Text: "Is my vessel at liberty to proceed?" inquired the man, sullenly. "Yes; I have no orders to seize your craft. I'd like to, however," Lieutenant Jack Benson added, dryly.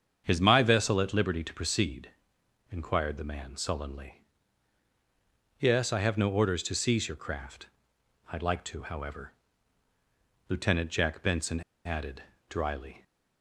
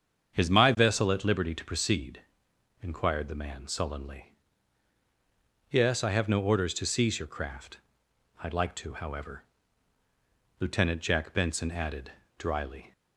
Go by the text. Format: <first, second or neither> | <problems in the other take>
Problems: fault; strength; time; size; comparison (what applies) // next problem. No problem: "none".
second | starts louder than the rest; strong; until 1.2 s; 7.5 dB; strong in the second // pauses between "Benson" and "added"; slight; at 11.6 s; 0.24 s long